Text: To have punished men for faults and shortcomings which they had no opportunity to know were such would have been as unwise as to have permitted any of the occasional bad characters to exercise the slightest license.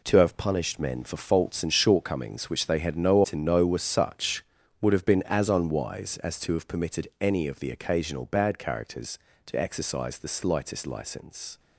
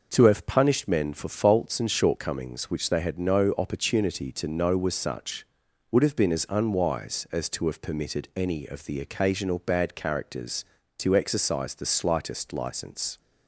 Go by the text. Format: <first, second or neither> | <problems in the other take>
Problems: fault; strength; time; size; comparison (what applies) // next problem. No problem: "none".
second | skips "opportunity"; at 3.2 s